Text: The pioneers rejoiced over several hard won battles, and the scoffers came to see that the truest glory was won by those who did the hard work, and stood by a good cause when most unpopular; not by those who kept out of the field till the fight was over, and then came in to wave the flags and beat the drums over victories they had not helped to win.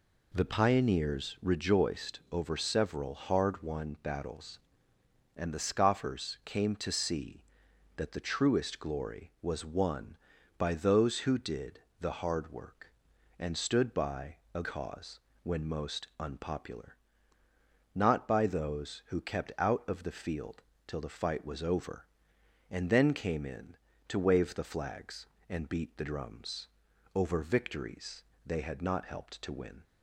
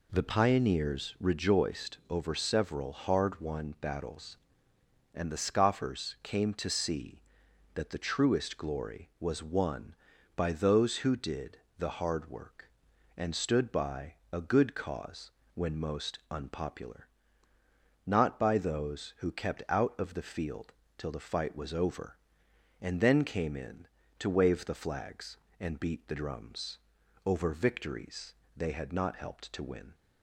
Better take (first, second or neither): second